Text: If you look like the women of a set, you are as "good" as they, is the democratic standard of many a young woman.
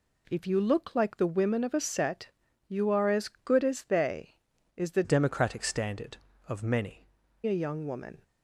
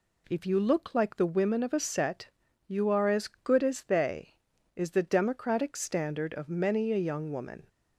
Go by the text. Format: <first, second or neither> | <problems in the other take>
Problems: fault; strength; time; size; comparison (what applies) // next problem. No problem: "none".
second | changes voice from "democratic" to "many"; from 5.0 to 7.0 s; 2.0 s long